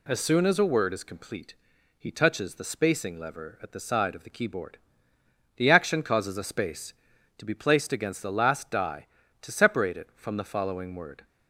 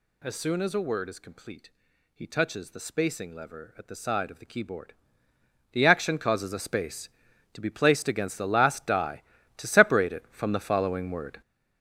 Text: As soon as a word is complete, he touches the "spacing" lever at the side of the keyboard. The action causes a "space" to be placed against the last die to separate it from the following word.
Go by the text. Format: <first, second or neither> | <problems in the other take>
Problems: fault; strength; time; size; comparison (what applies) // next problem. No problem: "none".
first | gets louder; strong; throughout; 9 dB